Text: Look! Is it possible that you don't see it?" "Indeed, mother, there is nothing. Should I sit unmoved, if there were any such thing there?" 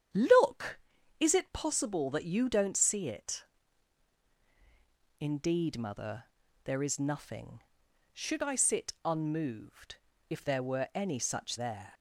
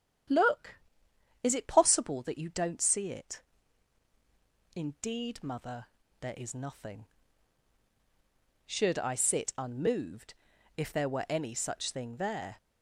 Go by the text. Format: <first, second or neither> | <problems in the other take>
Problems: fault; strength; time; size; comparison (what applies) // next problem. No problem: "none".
second | starts louder than the rest; strong; until 1.5 s; 9 dB; strong in the second // skips "thing"; at 11.5 s